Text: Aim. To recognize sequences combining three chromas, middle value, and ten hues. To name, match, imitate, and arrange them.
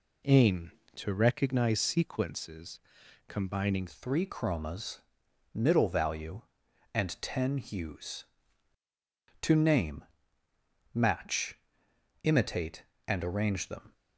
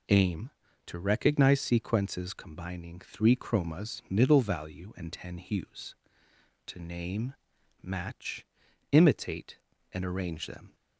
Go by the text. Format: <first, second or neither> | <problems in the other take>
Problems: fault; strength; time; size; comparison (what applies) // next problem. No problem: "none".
second | pauses between "sequences" and "combining"; noticeable; at 2.7 s; 0.48 s long // changes voice at "three"; from 3.8 s on; 10.1 s long